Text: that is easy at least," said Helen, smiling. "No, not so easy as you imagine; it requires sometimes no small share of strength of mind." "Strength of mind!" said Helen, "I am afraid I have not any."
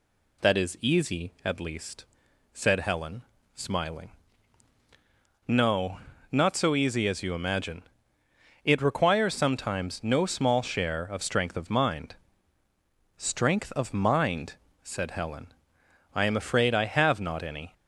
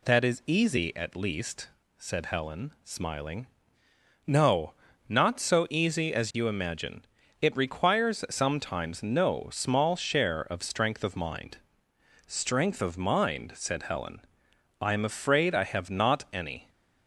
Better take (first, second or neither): neither